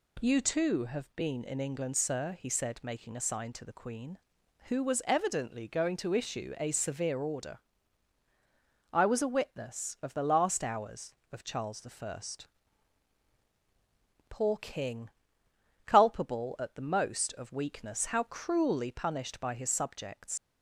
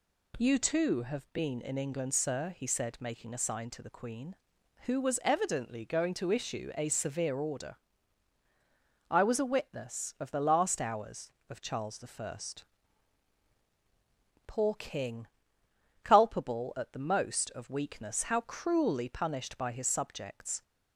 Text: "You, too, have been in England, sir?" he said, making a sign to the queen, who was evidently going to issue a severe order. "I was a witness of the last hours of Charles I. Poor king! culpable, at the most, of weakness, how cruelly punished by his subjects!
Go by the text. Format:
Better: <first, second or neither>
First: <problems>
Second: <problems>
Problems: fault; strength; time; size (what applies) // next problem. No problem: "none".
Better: second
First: leaves "subjects" unfinished; at 20.3 s; 80 ms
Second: none